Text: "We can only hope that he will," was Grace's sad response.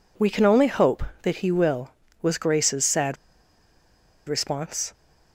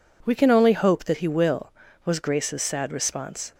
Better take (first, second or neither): second